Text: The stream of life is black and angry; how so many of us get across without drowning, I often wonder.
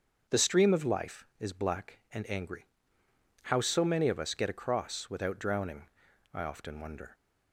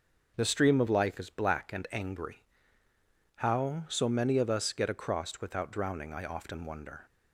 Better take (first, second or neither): neither